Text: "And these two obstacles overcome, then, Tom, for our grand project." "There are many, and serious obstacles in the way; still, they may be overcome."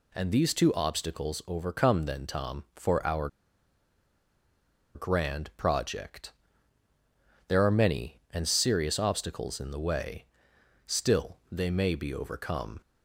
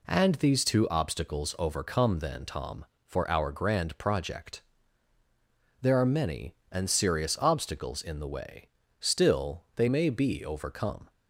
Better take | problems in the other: second | pauses between "our" and "grand"; strong; at 3.2 s; 1.6 s long

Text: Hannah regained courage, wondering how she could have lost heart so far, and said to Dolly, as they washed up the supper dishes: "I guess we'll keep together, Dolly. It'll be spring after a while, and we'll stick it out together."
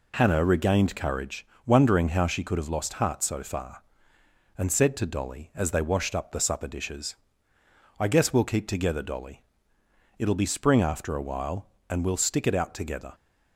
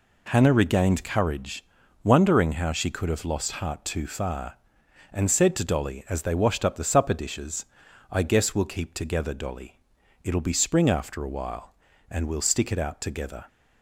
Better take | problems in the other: first | says "too" for "so"; at 3.8 s

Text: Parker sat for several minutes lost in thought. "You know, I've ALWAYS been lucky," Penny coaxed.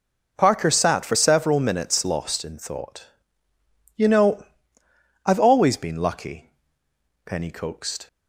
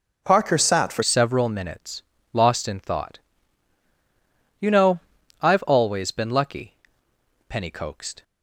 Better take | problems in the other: first | changes voice at "several"; from 1.0 s on; 7.2 s long // pauses between "minutes" and "lost"; slight; at 2.0 s; 0.32 s long

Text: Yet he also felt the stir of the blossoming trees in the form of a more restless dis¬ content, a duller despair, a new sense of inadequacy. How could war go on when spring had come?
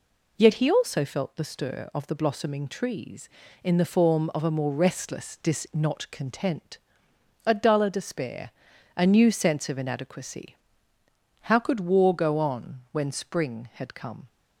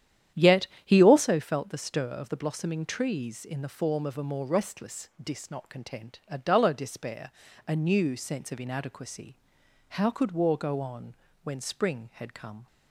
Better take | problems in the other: first | starts louder than the rest; strong; until 1.3 s; 10 dB // pauses between "Yet" and "he"; slight; at 0.6 s; 0.18 s long // pauses between "on" and "when"; slight; at 11.1 s; 0.30 s long

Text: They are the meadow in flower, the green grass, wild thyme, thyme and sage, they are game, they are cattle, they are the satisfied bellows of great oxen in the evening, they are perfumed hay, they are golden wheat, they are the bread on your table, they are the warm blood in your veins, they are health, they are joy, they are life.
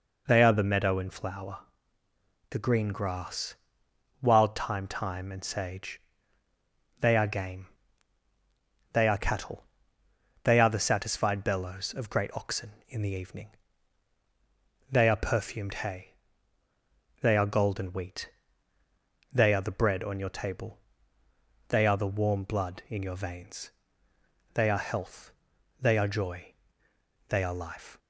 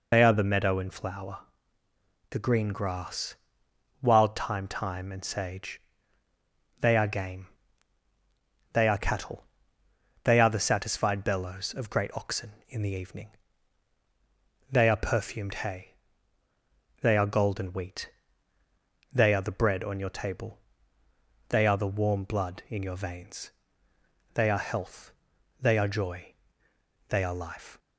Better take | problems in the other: first | loses the start of "They"; at 0.1 s; 50 ms

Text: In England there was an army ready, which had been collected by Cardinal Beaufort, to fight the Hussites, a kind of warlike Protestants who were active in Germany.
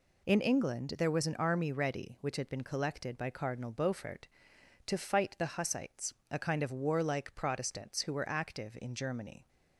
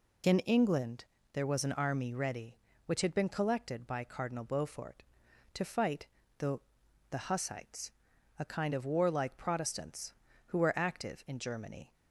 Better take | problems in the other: first | pauses between "England" and "there"; slight; at 1.0 s; 0.28 s long // pauses between "fight" and "the"; slight; at 6.0 s; 0.32 s long // says "the" twice; at 7.1 s

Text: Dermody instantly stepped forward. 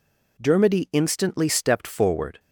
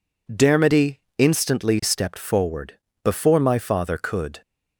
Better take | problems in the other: first | pauses between "Dermody" and "instantly"; slight; at 1.0 s; 0.18 s long // goes on to say "Before my father could"; from 3.0 s on; 1.3 s long

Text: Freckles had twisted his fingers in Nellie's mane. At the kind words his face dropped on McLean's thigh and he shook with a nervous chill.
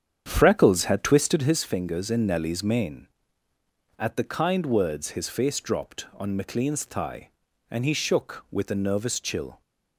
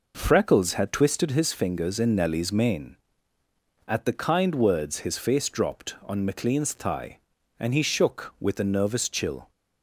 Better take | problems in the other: second | starts louder than the rest; strong; until 1.7 s; 8 dB

